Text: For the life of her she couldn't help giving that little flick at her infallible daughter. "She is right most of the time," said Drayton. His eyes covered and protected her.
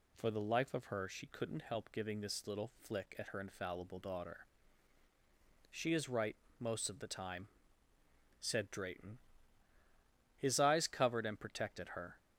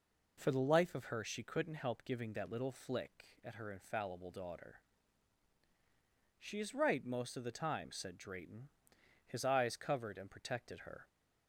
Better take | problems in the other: second | says "this" for "that"; at 2.1 s // pauses between "right" and "most"; slight; at 6.3 s; 0.22 s long

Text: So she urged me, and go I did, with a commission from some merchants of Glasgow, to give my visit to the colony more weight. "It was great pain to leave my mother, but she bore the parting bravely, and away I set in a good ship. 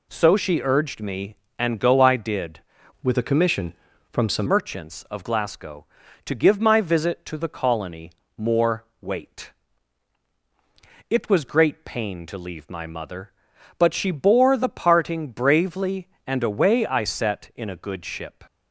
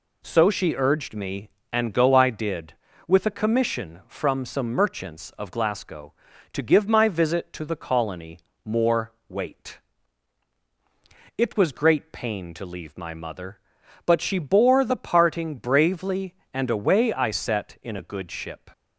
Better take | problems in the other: second | changes voice from "with" to "some"; from 3.0 to 4.4 s; 1.4 s long // pauses between "colony" and "more"; slight; at 8.1 s; 0.24 s long; slight in the second // pauses between "more" and "weight"; slight; at 8.8 s; 0.16 s long; slight in the second

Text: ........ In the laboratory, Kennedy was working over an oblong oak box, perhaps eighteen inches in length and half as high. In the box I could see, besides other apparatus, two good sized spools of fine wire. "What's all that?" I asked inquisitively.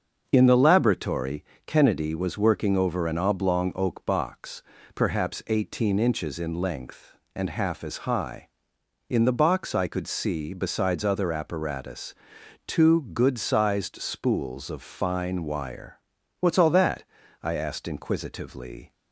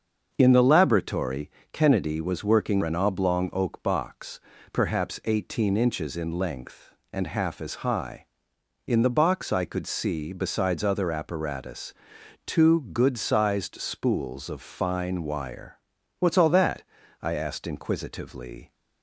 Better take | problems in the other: first | starts louder than the rest; until 1.3 s; 6.5 dB; also in the first // skips "over"; at 2.8 s

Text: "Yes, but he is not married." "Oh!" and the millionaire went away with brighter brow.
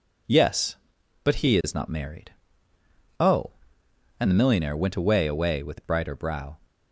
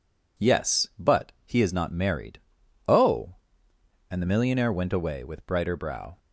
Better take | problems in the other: second | says "away" twice; at 5.2 s

